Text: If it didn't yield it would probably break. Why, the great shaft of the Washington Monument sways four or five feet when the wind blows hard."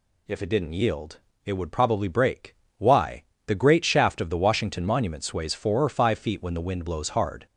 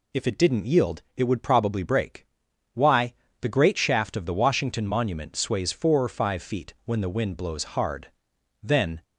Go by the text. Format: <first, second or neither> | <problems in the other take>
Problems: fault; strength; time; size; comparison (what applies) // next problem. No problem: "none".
first | pauses between "yield" and "it"; slight; at 1.0 s; 0.16 s long; slight in the first // goes on to say "Then"; slight; from 8.6 s on; 0.40 s long